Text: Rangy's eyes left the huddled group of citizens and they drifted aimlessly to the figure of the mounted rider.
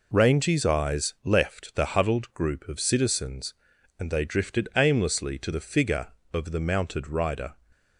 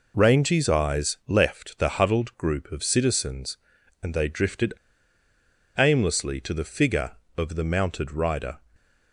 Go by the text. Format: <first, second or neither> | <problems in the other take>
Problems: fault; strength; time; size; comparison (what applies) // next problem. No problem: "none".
first | pauses between "drifted" and "aimlessly"; at 4.7 s; 1.0 s long